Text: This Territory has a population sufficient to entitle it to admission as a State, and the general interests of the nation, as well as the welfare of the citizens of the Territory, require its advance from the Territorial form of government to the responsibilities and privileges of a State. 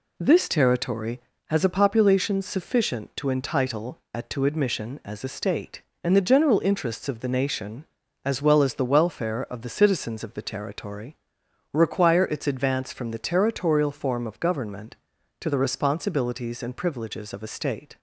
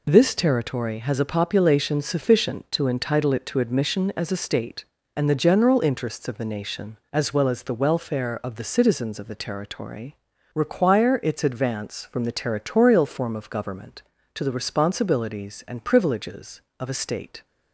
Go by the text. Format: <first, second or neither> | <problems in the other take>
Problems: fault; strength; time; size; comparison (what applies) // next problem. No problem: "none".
second | says "at" for "it"; at 4.1 s